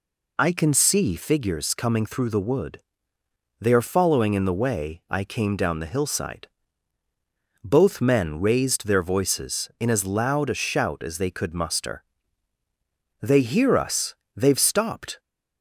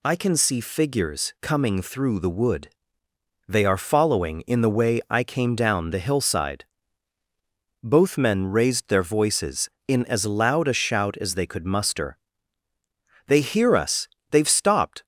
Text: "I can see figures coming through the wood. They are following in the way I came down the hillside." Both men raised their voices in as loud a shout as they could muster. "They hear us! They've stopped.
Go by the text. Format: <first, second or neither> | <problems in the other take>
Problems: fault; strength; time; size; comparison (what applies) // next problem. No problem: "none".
neither | none